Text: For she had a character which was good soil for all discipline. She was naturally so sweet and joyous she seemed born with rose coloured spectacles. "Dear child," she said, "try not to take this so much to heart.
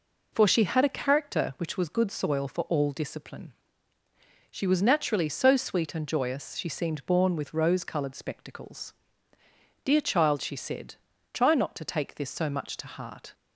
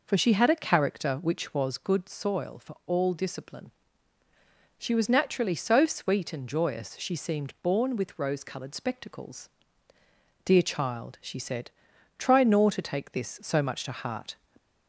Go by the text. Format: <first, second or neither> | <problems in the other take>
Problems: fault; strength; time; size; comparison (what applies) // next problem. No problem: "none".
first | says "nor" for "not"; at 12.4 s